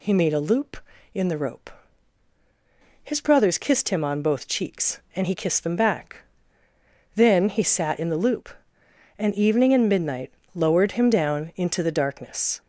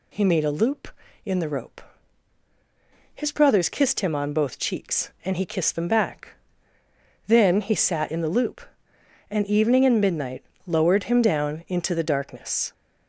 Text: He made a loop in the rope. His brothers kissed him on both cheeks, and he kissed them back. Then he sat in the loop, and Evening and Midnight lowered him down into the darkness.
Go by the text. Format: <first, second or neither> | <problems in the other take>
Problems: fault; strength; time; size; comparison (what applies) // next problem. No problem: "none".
neither | pauses between "Midnight" and "lowered"; slight; the same in both